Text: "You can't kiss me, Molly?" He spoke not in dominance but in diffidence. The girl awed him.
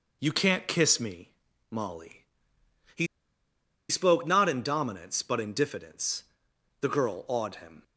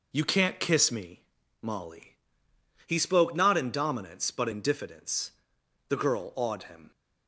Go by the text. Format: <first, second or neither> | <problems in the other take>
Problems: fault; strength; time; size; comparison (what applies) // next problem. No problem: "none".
second | pauses between "He" and "spoke"; noticeable; at 3.0 s; 0.83 s long